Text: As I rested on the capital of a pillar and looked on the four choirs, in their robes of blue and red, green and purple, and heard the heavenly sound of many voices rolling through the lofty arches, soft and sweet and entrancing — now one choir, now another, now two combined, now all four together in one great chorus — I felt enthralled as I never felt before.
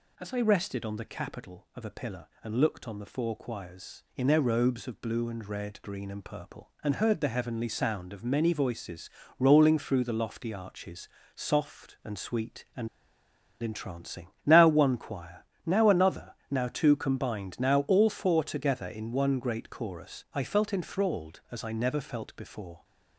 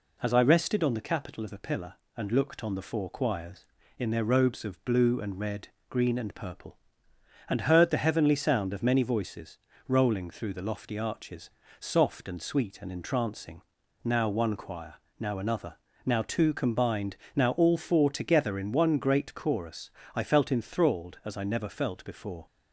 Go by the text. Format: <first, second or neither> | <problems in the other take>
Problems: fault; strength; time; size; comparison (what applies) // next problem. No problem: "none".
second | pauses between "voices" and "rolling"; slight; at 9.0 s; 0.30 s long; slight in the second // pauses between "and" and "entrancing"; noticeable; at 12.8 s; 0.73 s long